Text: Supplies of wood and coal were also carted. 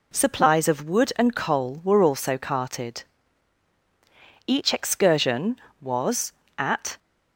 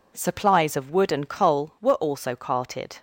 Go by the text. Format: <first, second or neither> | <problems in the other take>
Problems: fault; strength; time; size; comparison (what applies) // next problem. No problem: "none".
second | goes on to say "Each excursion was at"; strong; from 4.4 s on; 2.5 s long